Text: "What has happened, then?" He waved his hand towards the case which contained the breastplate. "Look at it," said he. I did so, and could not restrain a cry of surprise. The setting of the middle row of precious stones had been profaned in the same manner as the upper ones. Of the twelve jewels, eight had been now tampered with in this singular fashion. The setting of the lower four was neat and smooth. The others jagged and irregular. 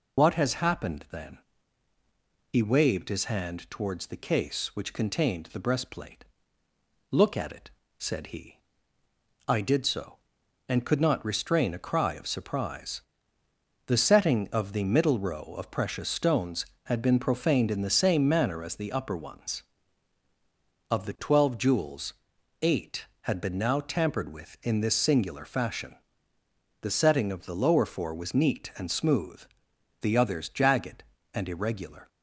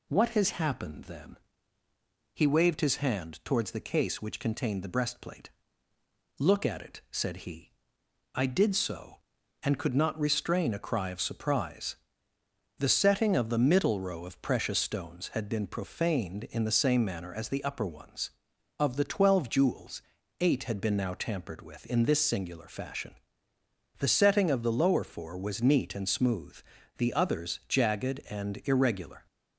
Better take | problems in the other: second | loses the start of "What"; at 0.1 s; 70 ms

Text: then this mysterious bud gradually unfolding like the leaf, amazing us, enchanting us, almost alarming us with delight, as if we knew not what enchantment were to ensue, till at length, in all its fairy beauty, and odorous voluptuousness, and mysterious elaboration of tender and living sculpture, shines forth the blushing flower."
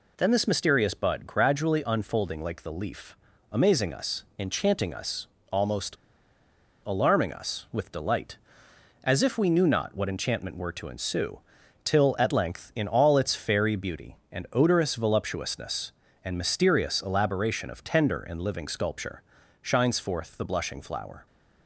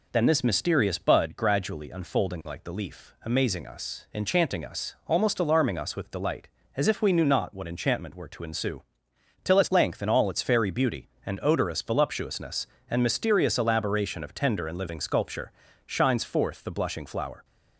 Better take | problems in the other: second | pauses between "almost" and "alarming"; noticeable; at 5.9 s; 0.90 s long

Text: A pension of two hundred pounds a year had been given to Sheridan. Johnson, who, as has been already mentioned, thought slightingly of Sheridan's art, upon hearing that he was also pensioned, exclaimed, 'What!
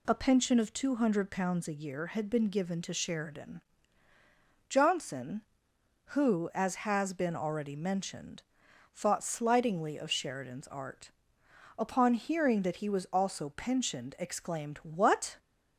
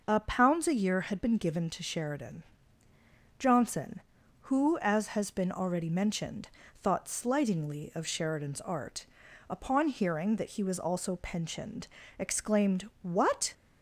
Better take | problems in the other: first | skips "pension of two hundred"; at 0.1 s

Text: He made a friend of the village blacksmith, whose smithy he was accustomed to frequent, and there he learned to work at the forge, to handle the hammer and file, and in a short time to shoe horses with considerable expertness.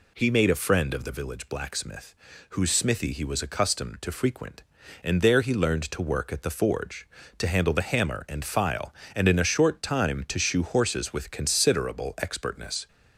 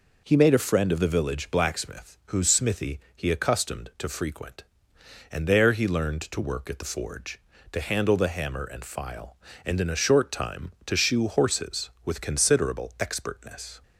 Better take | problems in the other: first | skips "was"; at 3.2 s

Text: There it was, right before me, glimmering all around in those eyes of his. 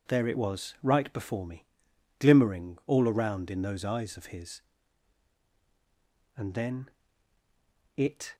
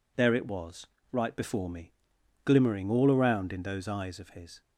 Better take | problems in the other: second | goes on to say "And then it"; strong; from 6.3 s on; 2.0 s long

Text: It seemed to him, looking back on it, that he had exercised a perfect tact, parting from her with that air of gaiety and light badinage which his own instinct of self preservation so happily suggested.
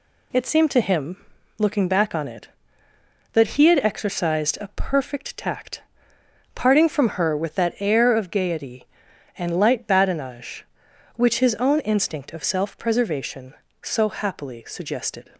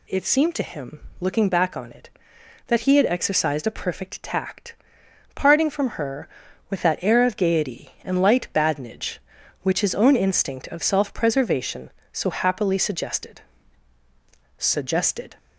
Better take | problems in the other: first | says "suggested" twice; at 14.5 s

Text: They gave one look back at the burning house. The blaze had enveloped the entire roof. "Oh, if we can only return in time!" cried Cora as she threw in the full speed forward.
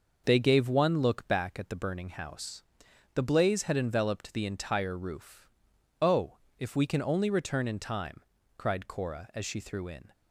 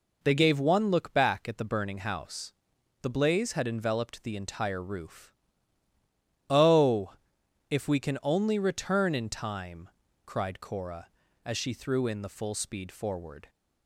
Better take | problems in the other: second | stops before "the full speed forward"; at 10.1 s

